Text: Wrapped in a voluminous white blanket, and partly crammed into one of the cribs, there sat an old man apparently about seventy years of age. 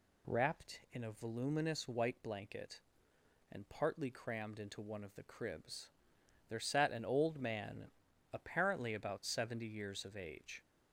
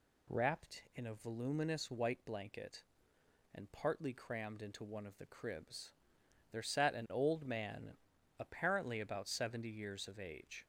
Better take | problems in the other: neither | pauses between "man" and "apparently"; the same in both

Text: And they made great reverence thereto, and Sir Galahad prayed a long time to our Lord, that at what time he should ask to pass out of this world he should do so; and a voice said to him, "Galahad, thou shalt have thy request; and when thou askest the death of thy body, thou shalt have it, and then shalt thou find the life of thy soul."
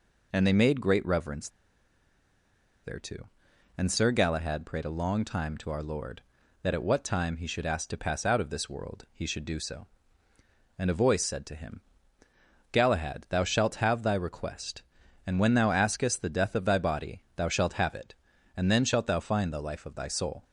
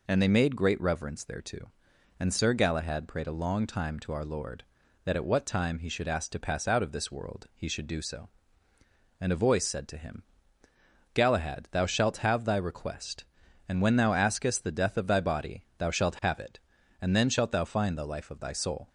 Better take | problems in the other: second | pauses between "reverence" and "thereto"; strong; at 1.4 s; 1.3 s long

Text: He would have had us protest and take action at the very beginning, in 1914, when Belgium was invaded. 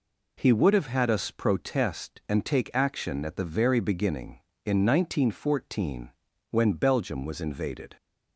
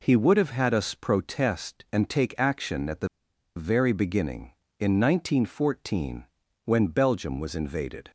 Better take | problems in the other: first | pauses between "the" and "very"; noticeable; at 3.0 s; 0.48 s long

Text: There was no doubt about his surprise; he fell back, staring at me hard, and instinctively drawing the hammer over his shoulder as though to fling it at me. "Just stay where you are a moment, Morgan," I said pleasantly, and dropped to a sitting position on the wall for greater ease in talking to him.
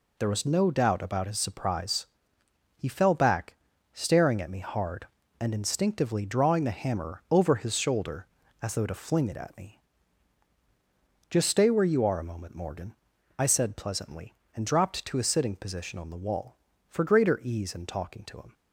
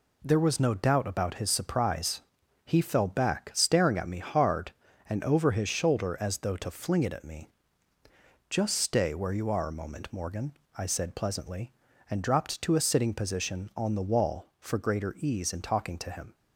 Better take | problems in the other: first | skips "instinctively drawing the hammer"; at 5.2 s

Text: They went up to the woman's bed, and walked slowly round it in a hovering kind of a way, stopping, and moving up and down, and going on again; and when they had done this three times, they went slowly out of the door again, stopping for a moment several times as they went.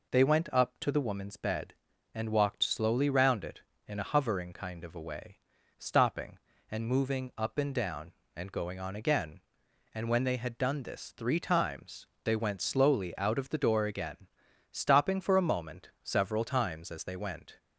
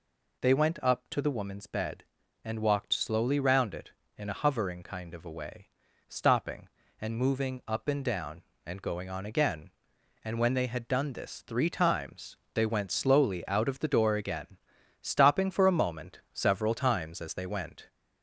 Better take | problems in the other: first | gets louder; slight; throughout; 2 dB

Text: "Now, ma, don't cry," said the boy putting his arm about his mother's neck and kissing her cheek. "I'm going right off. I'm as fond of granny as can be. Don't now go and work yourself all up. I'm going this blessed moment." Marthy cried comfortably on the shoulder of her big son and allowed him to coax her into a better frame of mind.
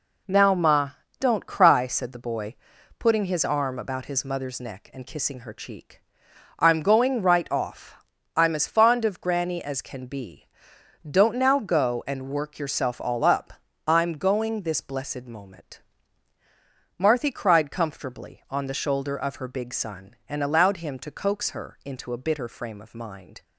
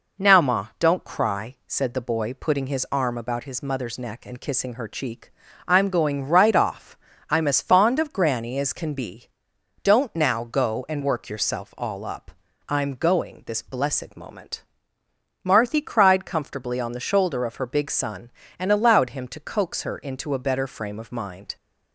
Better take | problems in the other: second | pauses between "boy" and "putting"; at 2.5 s; 0.42 s long // says "bitter" for "better"; at 22.2 s

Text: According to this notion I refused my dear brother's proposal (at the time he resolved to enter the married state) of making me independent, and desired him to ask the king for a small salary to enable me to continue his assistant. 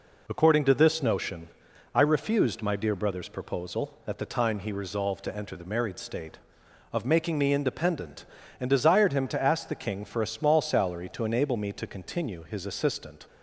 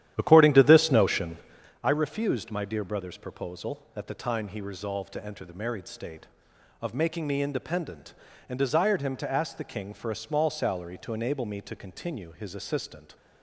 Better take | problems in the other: first | starts louder than the rest; strong; until 1.7 s; 11.5 dB // pauses between "notion" and "I"; noticeable; at 1.3 s; 0.46 s long; noticeable in the first

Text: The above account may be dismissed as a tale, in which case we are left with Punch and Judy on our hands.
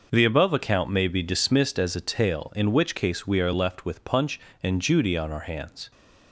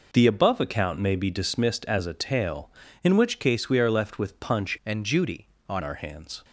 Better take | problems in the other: first | changes voice from "and" to "on"; from 4.8 to 5.8 s; 1.0 s long

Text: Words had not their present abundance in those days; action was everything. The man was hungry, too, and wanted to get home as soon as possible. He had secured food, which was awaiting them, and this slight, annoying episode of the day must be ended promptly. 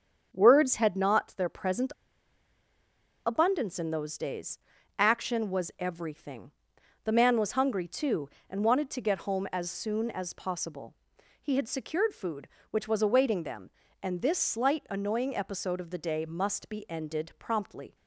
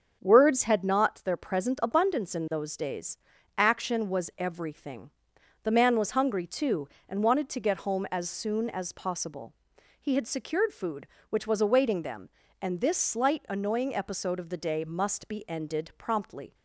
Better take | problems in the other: second | starts louder than the rest; strong; until 1.3 s; 7.5 dB; strong in the second // pauses between "present" and "abundance"; strong; at 1.9 s; 1.3 s long

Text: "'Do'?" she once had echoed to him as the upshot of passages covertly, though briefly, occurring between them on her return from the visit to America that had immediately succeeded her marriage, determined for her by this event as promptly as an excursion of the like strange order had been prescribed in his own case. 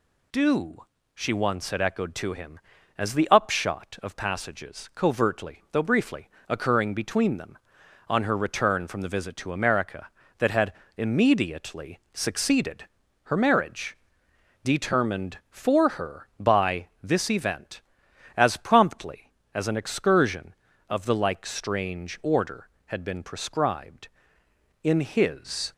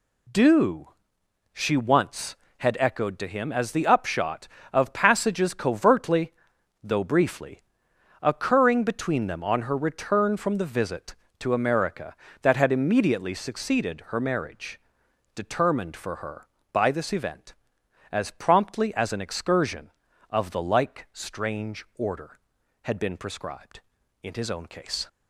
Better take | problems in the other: second | pauses between "had" and "immediately"; slight; at 10.7 s; 0.24 s long // pauses between "succeeded" and "her"; at 12.8 s; 0.40 s long // pauses between "by" and "this"; slight; at 16.8 s; 0.16 s long // stops before "own case"; at 25.7 s

